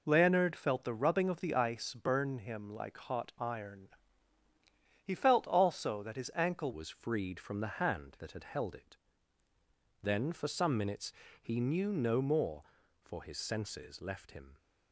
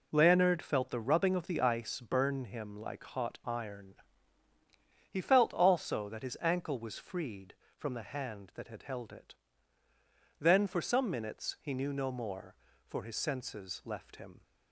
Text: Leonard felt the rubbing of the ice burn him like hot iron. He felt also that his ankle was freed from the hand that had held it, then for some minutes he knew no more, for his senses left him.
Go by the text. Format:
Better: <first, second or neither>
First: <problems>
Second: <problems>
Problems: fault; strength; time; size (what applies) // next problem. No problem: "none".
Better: second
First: changes voice at "was"; from 6.7 s on; 7.8 s long // pauses between "minutes" and "he"; slight; at 11.1 s; 0.30 s long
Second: none